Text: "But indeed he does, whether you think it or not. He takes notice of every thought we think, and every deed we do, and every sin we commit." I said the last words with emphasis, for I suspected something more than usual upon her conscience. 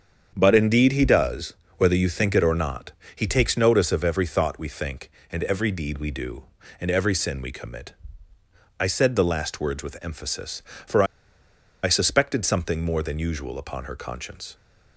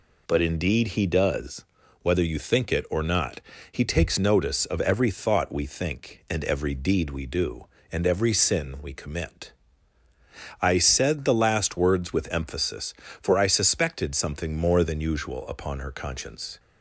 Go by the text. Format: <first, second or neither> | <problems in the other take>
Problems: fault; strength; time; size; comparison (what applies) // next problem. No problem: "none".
second | starts louder than the rest; strong; until 1.3 s; 7.5 dB // pauses between "for" and "I"; noticeable; at 11.0 s; 0.79 s long